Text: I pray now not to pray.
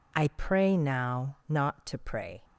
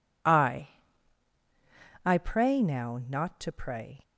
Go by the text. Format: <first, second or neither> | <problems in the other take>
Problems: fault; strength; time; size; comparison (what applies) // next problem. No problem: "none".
first | says "I" twice; at 2.0 s